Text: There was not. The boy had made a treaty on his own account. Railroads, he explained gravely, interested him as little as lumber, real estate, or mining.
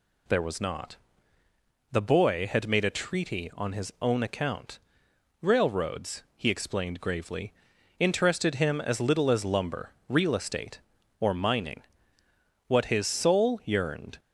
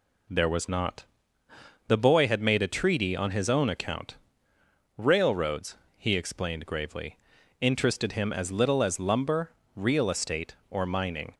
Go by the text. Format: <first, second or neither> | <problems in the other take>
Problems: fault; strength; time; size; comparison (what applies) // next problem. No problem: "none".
second | goes on to say "What his soul yearned"; from 12.6 s on; 1.5 s long